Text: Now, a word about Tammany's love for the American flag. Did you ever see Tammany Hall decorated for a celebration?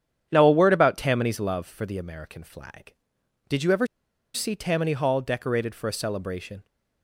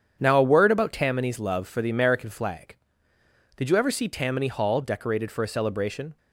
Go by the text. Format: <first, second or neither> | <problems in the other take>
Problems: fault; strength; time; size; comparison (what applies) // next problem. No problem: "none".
second | starts louder than the rest; strong; until 1.3 s; 9 dB; strong in the second // pauses between "ever" and "see"; noticeable; at 3.8 s; 0.48 s long